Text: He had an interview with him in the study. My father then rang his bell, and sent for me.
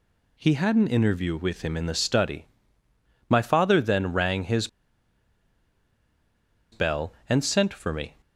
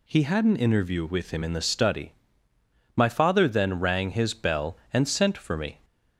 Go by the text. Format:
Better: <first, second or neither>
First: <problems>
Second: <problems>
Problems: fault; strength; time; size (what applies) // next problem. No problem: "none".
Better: second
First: pauses between "his" and "bell"; strong; at 4.6 s; 2.0 s long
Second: none